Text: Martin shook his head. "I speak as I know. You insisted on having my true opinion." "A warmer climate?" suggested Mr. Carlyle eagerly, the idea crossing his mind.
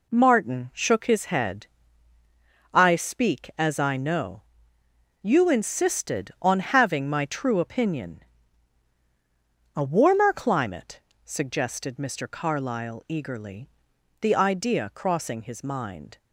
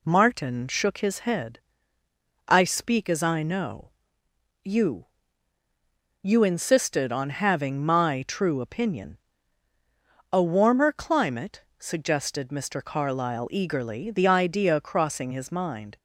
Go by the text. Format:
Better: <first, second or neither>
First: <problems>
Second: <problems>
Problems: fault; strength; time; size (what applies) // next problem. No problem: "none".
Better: first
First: none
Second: says "You" twice; at 6.2 s